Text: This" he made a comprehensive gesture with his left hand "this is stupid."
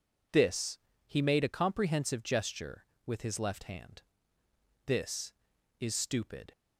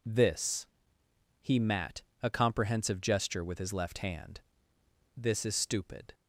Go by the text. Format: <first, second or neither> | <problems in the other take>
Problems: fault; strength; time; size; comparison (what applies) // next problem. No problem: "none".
first | pauses between "This" and "he"; noticeable; at 0.6 s; 0.76 s long; slight in the first // says "mat" for "made"; at 1.5 s // pauses between "hand" and "this"; noticeable; at 4.3 s; 0.78 s long; noticeable in the first